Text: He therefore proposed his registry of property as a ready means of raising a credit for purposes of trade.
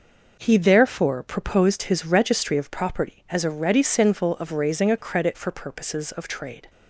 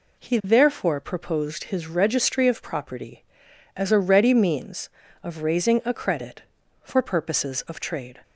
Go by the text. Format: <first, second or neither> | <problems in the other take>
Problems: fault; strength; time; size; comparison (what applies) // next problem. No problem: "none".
second | says "sinful" for "means"; at 3.8 s